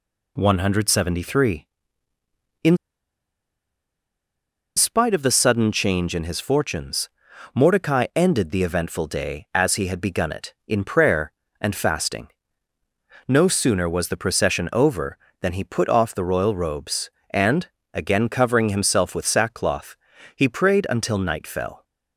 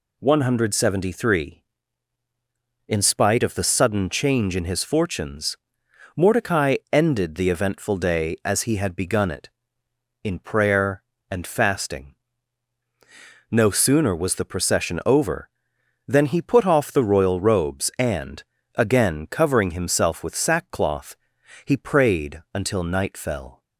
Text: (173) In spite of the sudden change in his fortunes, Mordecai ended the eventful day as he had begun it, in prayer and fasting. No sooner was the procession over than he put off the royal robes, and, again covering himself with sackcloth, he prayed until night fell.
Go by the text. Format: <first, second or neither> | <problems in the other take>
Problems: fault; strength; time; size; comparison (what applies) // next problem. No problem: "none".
second | pauses between "In" and "spite"; strong; at 2.7 s; 2.0 s long